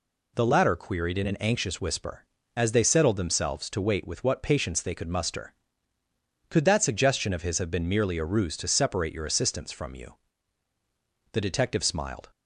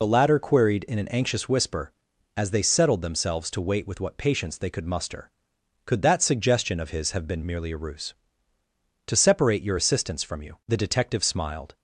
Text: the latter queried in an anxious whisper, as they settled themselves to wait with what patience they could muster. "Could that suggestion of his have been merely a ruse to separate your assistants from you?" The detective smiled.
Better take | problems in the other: first | loses the start of "the"; at 0.0 s; 40 ms

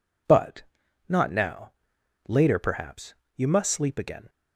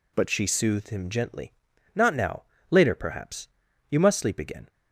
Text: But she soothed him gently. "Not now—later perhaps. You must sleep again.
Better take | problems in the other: second | skips "she soothed him gently"; at 0.8 s

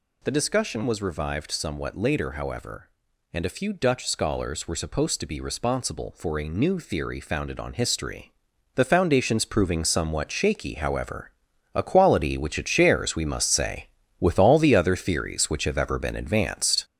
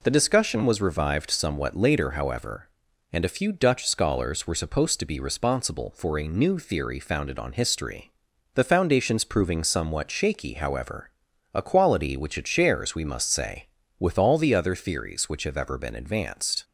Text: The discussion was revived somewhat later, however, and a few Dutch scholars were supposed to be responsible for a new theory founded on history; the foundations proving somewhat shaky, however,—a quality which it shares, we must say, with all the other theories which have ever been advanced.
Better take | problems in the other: second | gets louder; noticeable; throughout; 5.5 dB

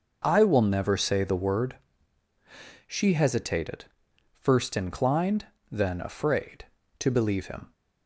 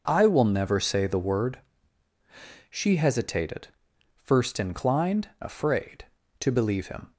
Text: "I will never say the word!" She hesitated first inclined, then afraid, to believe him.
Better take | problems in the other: first | pauses between "hesitated" and "first"; noticeable; at 3.6 s; 0.48 s long; noticeable in the first // skips "then"; at 5.3 s

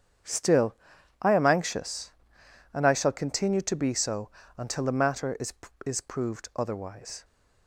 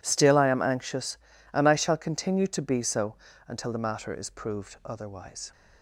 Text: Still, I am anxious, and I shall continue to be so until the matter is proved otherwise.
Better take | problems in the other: second | starts louder than the rest; strong; until 1.7 s; 8 dB // pauses between "so" and "until"; slight; at 4.3 s; 0.26 s long; slight in the second // says "is" twice; at 5.8 s

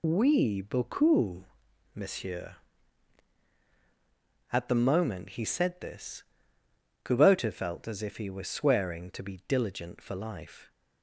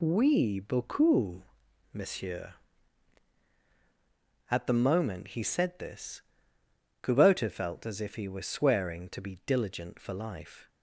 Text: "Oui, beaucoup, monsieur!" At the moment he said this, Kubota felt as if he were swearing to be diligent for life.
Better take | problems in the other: second | loses the start of "Oui"; at 0.0 s; 20 ms

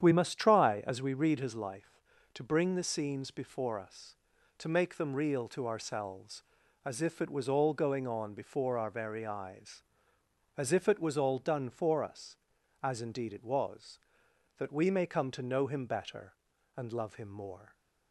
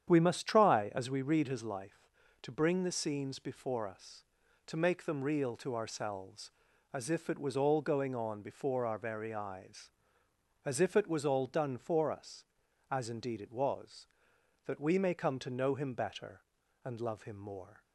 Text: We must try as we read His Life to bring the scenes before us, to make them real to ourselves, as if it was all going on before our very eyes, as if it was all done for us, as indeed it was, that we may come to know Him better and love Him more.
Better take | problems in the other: neither | starts louder than the rest; strong; the same in both

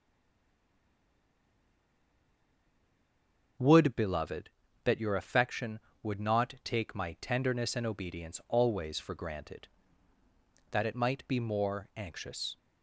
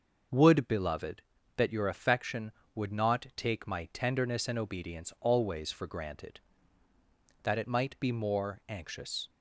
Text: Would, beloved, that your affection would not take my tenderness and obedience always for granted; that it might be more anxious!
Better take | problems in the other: second | stays silent before the first word; strong; until 3.5 s; 3.5 s long // starts louder than the rest; until 4.9 s; 6.5 dB; also in the second

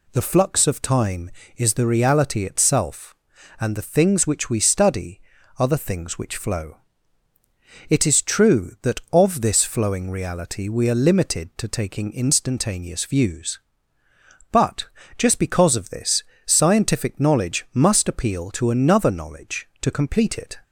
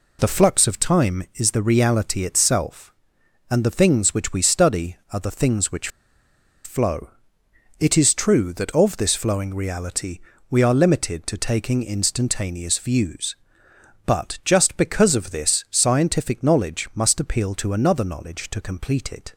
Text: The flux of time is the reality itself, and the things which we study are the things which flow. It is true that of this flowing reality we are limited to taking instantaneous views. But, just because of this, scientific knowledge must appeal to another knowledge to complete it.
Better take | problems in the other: first | pauses between "which" and "flow"; noticeable; at 5.8 s; 0.76 s long // pauses between "reality" and "we"; slight; at 10.2 s; 0.30 s long

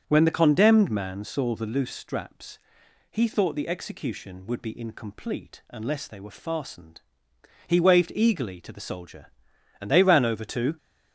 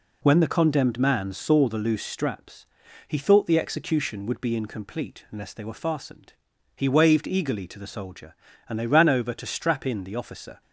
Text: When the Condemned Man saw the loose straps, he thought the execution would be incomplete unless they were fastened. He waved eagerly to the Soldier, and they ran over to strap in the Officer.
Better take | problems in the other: second | starts louder than the rest; strong; until 1.0 s; 7.5 dB // stops before "strap in the Officer"; at 10.7 s

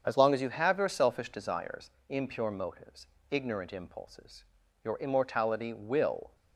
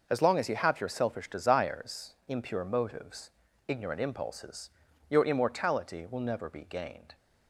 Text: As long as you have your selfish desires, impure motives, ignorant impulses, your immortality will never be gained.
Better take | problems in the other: second | starts louder than the rest; strong; until 1.0 s; 7.5 dB // stops before "never be gained"; at 6.3 s

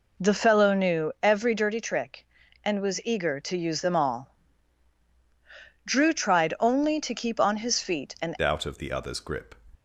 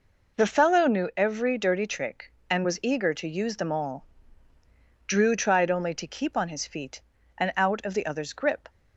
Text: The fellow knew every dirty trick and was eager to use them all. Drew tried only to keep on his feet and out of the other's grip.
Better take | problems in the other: second | changes voice at "out"; from 8.4 s on; 1.1 s long

